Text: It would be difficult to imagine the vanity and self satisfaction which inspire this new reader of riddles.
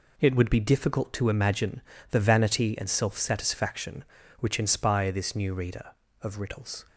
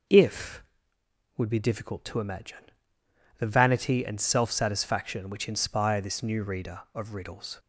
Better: first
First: pauses between "imagine" and "the"; slight; at 1.8 s; 0.28 s long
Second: says "If" for "It"; at 0.0 s // pauses between "imagine" and "the"; noticeable; at 2.7 s; 0.68 s long

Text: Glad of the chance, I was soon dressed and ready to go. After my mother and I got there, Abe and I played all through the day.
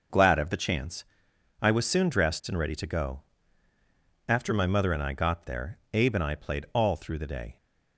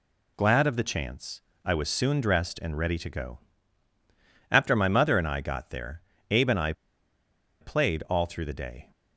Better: first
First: none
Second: pauses between "I" and "played"; noticeable; at 6.7 s; 0.88 s long

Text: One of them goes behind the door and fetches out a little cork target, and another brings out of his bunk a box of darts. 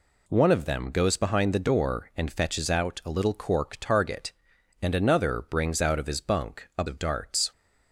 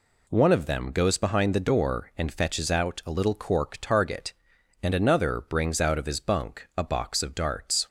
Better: second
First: skips "box"; at 6.8 s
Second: none

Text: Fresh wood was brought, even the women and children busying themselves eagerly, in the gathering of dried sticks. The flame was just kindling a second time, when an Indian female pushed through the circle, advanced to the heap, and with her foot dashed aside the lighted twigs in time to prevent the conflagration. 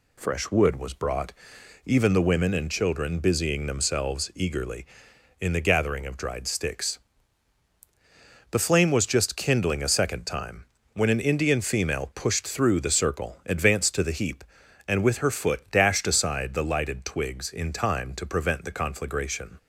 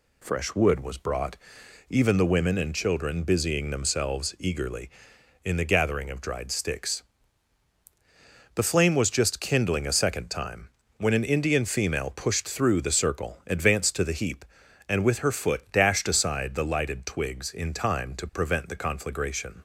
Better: neither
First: none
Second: none

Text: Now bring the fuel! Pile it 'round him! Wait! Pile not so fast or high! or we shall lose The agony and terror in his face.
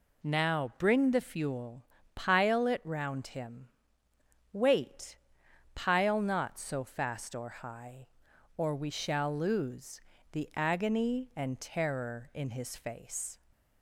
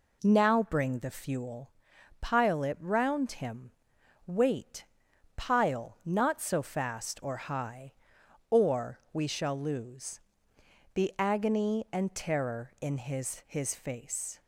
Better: first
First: pauses between "lose" and "The"; slight; at 10.0 s; 0.32 s long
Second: pauses between "or" and "we"; slight; at 8.9 s; 0.16 s long // pauses between "lose" and "The"; noticeable; at 10.2 s; 0.72 s long // says "his" twice; at 13.4 s

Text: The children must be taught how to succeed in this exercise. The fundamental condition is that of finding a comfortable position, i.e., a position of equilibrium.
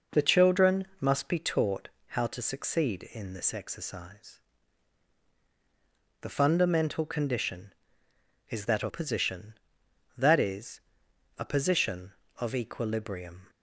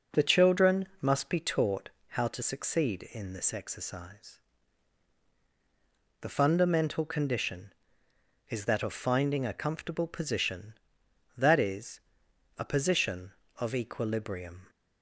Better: second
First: pauses between "taught" and "how"; slight; at 1.8 s; 0.20 s long // skips "finding a comfortable"; at 8.8 s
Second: pauses between "taught" and "how"; slight; at 1.8 s; 0.20 s long

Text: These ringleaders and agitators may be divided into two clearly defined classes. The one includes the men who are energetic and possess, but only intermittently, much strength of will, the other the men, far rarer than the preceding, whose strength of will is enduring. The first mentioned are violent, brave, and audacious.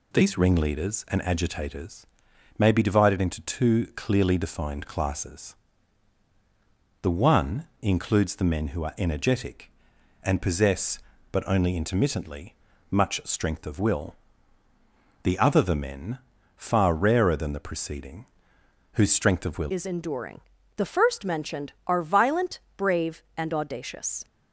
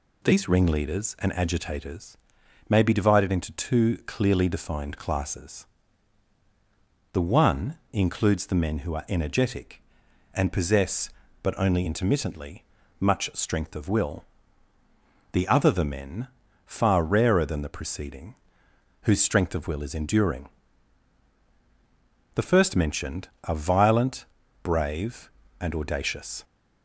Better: second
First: pauses between "agitators" and "may"; noticeable; at 2.0 s; 0.52 s long // changes voice at "is"; from 19.6 s on; 4.6 s long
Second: pauses between "agitators" and "may"; noticeable; at 2.1 s; 0.52 s long

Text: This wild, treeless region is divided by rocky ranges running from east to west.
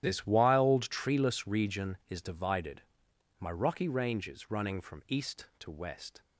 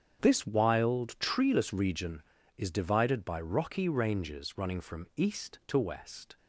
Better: second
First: starts louder than the rest; strong; until 1.0 s; 11.5 dB // says "my" for "by"; at 3.4 s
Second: starts louder than the rest; strong; until 1.2 s; 8 dB

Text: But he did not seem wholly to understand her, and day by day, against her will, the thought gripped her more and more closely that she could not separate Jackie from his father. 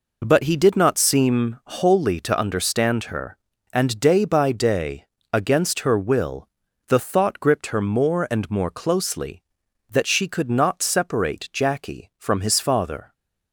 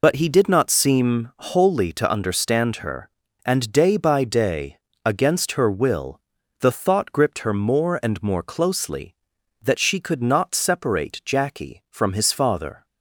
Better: first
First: none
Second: loses the start of "But"; at 0.0 s; 95 ms

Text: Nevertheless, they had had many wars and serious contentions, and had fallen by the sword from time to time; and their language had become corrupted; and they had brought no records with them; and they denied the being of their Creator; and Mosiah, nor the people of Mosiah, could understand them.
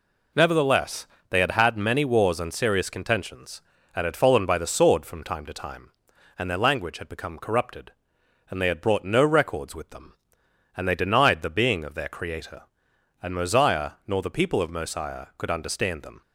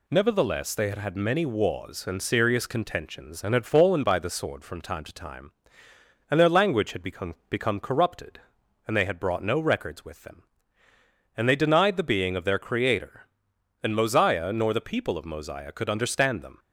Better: first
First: none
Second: says "become" twice; at 7.4 s

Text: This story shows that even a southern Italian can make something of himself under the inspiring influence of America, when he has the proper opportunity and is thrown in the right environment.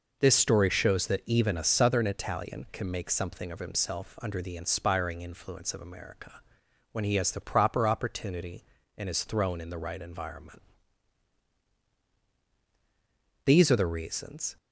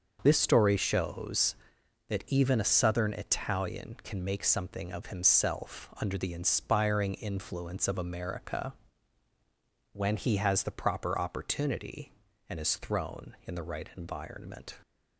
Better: second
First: goes on to say "These are the reasons"; noticeable; from 13.4 s on; 1.1 s long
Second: none

